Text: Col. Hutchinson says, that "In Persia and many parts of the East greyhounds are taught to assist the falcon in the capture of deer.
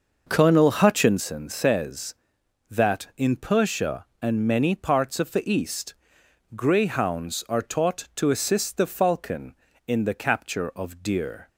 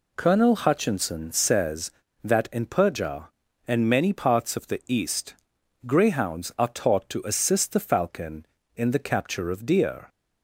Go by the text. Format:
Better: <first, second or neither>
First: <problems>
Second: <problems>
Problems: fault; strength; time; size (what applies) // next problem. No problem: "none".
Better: second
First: starts louder than the rest; noticeable; until 1.3 s; 6 dB // pauses between "East" and "greyhounds"; noticeable; at 5.9 s; 0.63 s long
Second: pauses between "East" and "greyhounds"; noticeable; at 5.3 s; 0.52 s long